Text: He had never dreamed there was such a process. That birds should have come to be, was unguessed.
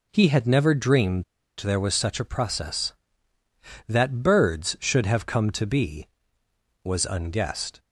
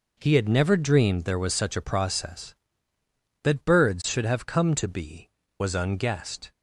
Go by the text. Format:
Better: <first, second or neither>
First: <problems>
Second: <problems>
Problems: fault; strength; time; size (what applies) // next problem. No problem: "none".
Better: second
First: pauses between "dreamed" and "there"; slight; at 1.2 s; 0.34 s long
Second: none